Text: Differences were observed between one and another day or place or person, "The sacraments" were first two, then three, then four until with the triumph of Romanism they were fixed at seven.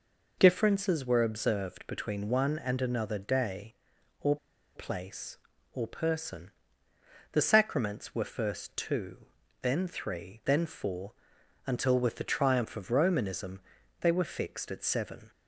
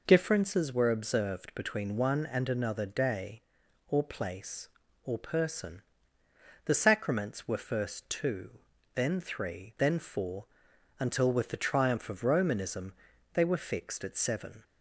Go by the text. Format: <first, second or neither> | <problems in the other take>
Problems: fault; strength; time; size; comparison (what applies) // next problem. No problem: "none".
second | pauses between "or" and "place"; at 4.3 s; 0.39 s long // pauses between "four" and "until"; noticeable; at 11.1 s; 0.52 s long; noticeable in the second // pauses between "Romanism" and "they"; at 13.6 s; 0.40 s long; also in the second